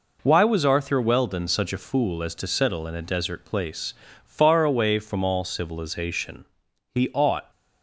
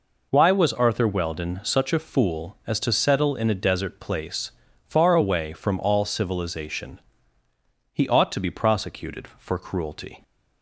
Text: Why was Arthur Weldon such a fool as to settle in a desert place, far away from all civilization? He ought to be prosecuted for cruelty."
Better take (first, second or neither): second